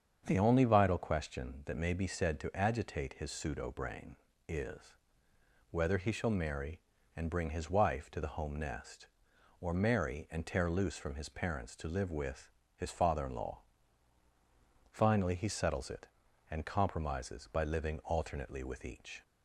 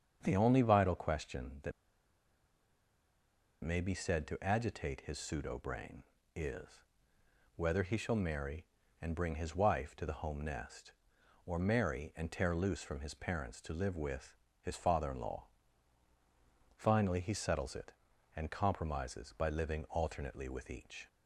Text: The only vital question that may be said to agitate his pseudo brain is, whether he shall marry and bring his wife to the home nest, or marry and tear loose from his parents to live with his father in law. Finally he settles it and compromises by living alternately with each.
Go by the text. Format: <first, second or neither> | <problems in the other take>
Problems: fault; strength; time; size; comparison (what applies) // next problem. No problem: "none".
first | starts louder than the rest; strong; until 1.2 s; 7.5 dB; strong in the first // pauses between "that" and "may"; strong; at 1.7 s; 1.9 s long // pauses between "with" and "his"; slight; at 14.3 s; 0.24 s long; slight in the first